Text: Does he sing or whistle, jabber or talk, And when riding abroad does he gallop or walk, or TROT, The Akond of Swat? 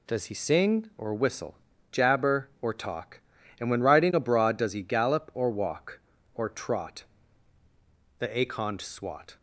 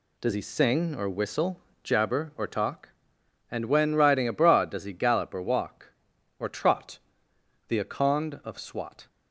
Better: second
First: skips "of"; at 8.8 s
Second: none

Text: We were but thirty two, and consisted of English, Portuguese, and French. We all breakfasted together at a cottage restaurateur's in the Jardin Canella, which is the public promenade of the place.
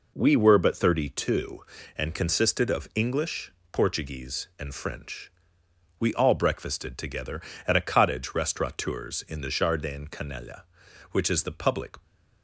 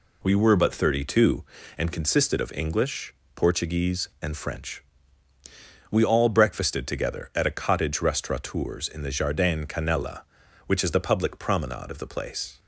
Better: second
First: stops before "promenade of the place"; at 12.0 s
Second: none

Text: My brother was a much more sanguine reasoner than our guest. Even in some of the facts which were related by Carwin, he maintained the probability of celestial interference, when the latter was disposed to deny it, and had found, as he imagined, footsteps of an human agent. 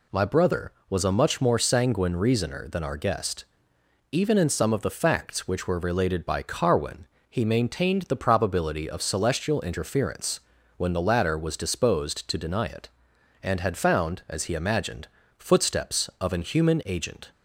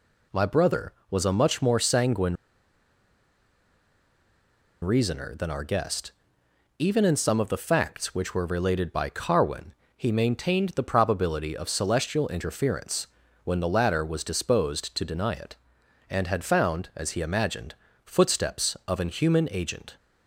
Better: first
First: none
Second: pauses between "sanguine" and "reasoner"; strong; at 2.3 s; 2.4 s long

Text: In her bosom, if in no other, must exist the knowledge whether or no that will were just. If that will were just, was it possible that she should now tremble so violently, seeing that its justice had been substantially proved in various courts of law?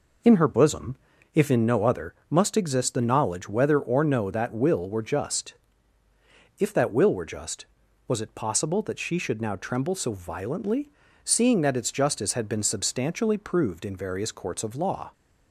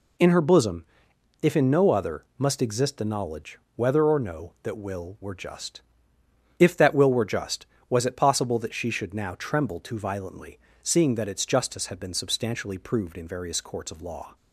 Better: first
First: none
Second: pauses between "knowledge" and "whether"; slight; at 3.5 s; 0.16 s long // says "too" for "so"; at 9.7 s

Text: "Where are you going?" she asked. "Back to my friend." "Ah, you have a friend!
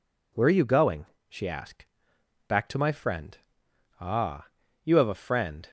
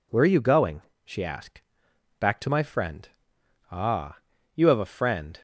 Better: neither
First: none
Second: none

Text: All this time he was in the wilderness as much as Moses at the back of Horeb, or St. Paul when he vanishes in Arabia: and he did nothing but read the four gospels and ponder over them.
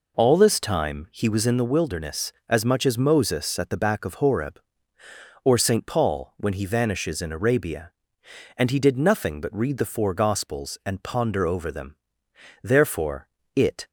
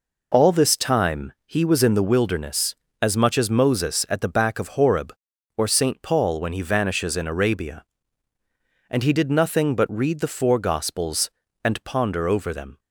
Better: second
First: goes on to say "Therefore it"; noticeable; from 12.6 s on; 1.2 s long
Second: none

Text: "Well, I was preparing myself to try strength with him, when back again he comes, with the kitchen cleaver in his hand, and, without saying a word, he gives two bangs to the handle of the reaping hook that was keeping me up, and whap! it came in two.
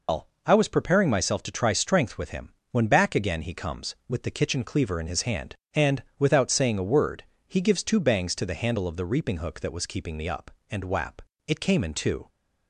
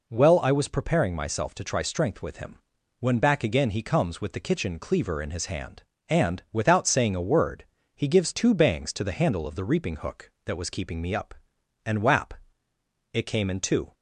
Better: second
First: loses the start of "Well"; at 0.0 s; 165 ms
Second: none

